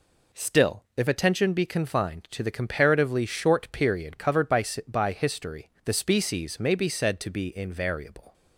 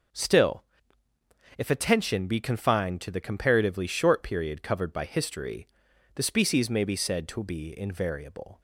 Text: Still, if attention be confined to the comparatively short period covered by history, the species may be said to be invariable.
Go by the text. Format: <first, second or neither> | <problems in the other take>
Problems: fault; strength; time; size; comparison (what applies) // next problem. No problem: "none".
second | says "by" twice; at 4.8 s